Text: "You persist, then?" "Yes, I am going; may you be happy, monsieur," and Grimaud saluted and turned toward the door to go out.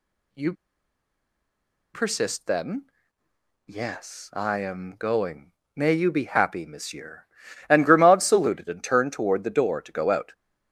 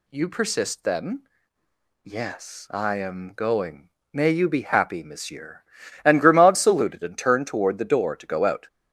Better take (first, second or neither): second